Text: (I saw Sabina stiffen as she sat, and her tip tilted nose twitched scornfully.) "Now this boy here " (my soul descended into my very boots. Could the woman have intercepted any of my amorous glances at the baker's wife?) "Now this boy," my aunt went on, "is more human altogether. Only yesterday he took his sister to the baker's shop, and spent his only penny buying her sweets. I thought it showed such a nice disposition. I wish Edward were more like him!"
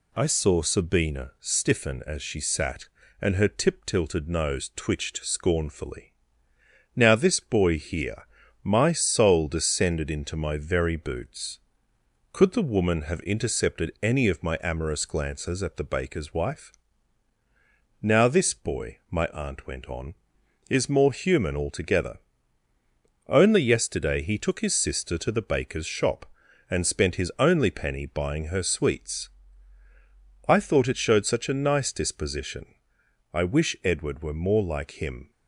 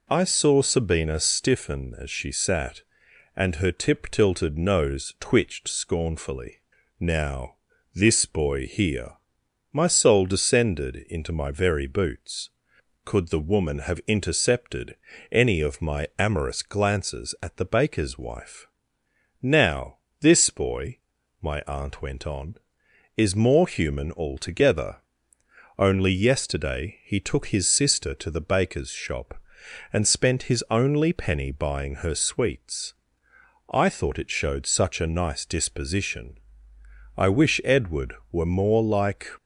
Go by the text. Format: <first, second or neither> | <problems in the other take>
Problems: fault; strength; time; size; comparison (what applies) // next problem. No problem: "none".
first | pauses between "Now" and "this"; at 7.5 s; 0.38 s long // pauses between "intercepted" and "any"; slight; at 14.9 s; 0.36 s long // pauses between "Now" and "this"; slight; at 19.9 s; 0.22 s long // stops before "him"; at 39.3 s